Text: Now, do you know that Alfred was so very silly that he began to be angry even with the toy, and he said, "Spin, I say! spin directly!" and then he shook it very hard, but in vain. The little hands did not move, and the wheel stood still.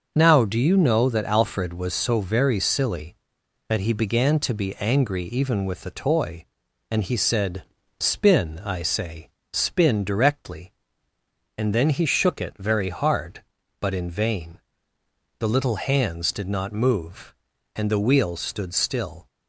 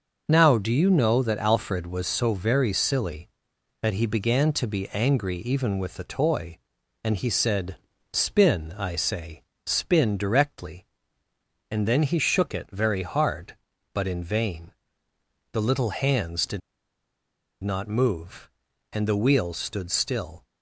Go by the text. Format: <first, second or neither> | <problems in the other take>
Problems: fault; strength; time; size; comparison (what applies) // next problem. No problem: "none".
first | starts louder than the rest; noticeable; until 1.2 s; 6 dB; noticeable in the first // pauses between "did" and "not"; at 16.6 s; 1.0 s long